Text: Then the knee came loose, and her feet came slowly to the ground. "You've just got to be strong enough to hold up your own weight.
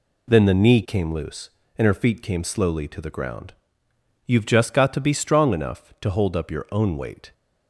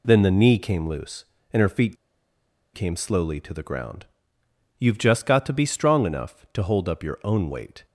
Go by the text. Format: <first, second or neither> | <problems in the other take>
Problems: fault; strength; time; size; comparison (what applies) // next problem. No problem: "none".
first | pauses between "feet" and "came"; noticeable; at 1.9 s; 0.79 s long